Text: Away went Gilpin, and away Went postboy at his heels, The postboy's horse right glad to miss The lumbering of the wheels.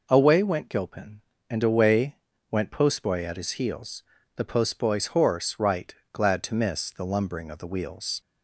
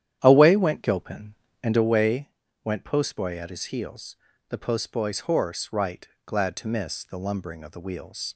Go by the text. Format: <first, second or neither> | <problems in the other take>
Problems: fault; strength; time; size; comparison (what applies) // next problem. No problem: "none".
first | starts louder than the rest; strong; until 1.9 s; 10.5 dB // pauses between "away" and "Went"; slight; at 2.2 s; 0.34 s long; slight in the first // pauses between "right" and "glad"; slight; at 6.0 s; 0.18 s long; slight in the first